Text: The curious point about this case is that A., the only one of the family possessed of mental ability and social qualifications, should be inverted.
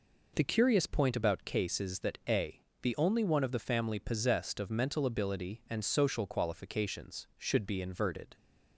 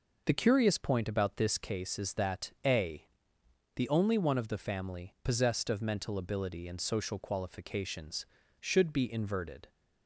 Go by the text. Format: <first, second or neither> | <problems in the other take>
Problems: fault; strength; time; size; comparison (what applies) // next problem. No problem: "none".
second | skips "this"; at 1.4 s